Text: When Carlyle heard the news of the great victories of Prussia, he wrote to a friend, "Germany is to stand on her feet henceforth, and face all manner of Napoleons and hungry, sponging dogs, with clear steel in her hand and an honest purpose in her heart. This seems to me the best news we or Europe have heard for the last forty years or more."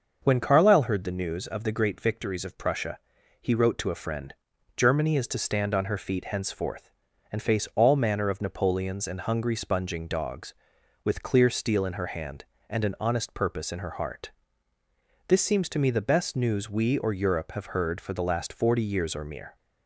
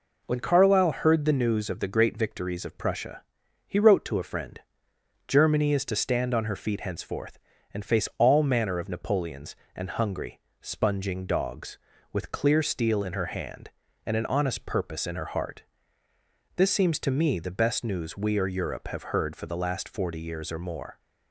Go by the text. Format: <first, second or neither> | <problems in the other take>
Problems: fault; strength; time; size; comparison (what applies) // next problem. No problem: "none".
second | starts louder than the rest; until 1.2 s; 6.5 dB // says "mere" for "more"; at 19.2 s